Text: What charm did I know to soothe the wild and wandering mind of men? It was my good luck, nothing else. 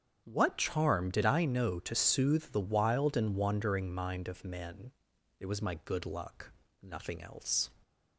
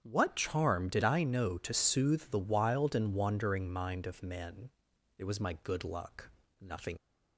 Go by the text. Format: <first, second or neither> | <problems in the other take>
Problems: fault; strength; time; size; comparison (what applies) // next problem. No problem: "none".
first | starts louder than the rest; strong; until 1.0 s; 8 dB; strong in the first // stops before "else"; at 6.9 s